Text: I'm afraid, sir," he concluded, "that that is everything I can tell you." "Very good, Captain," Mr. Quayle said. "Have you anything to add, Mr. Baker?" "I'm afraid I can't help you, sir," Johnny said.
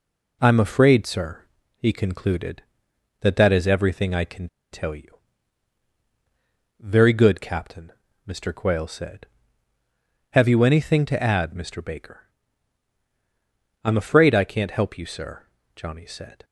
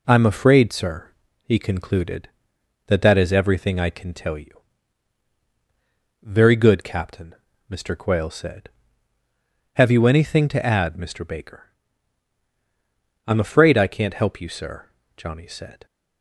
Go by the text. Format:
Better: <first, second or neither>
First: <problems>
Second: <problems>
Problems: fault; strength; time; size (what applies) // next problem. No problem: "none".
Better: second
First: pauses between "can" and "tell"; slight; at 4.4 s; 0.22 s long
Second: none